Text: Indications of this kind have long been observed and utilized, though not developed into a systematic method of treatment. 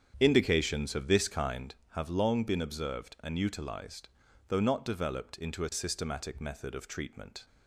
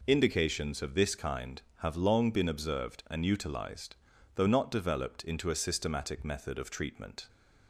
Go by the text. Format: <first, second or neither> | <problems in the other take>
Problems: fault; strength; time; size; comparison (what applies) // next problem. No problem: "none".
second | starts louder than the rest; strong; until 1.7 s; 8.5 dB